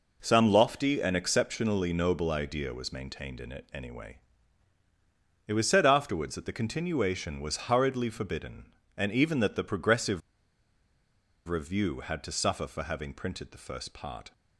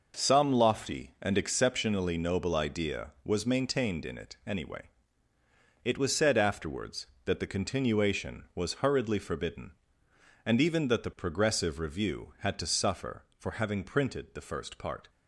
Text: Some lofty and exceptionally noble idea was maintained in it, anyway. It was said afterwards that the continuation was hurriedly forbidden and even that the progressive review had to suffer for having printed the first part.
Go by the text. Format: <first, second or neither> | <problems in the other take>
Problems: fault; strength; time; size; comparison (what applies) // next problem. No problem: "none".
second | pauses between "progressive" and "review"; strong; at 10.2 s; 1.2 s long